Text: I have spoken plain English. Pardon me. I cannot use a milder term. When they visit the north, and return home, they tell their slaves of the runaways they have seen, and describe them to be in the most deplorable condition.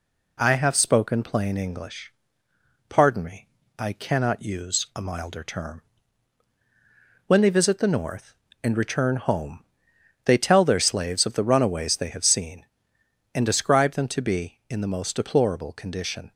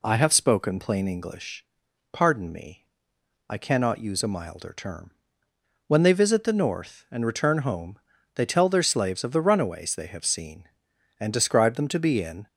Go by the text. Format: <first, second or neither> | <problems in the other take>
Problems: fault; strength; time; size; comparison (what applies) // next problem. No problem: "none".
first | stops before "the most deplorable condition"; at 12.4 s